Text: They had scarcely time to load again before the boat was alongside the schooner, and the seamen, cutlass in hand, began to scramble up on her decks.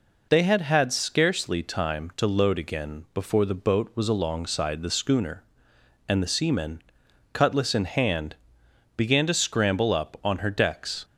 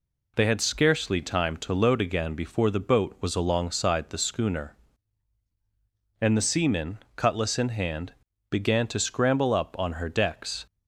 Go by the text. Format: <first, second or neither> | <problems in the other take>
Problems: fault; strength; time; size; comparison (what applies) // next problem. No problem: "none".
second | says "had" twice; at 0.6 s